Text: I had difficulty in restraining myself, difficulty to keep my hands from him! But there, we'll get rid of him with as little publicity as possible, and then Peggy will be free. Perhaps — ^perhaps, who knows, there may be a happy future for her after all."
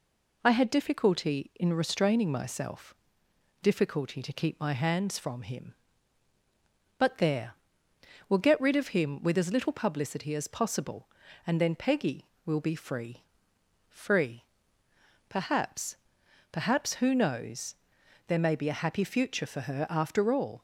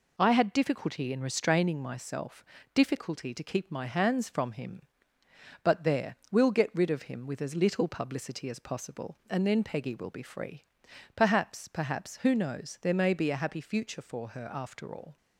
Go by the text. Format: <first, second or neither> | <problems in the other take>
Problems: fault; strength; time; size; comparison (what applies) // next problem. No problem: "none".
second | says "free" twice; at 13.8 s